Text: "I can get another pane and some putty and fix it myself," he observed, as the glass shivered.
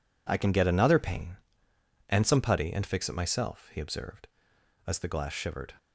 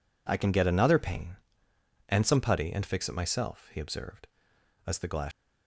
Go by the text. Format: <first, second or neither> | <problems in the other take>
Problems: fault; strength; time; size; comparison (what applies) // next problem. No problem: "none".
first | stops before "shivered"; at 5.3 s